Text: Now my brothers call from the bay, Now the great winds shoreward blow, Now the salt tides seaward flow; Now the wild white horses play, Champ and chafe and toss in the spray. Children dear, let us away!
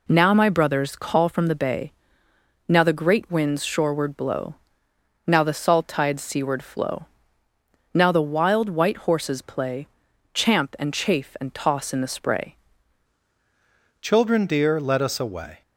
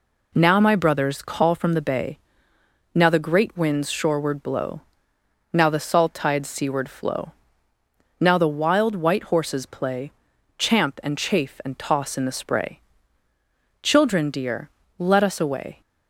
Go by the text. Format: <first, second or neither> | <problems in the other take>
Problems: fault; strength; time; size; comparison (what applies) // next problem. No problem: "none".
second | changes voice at "Children"; from 13.9 s on; 1.7 s long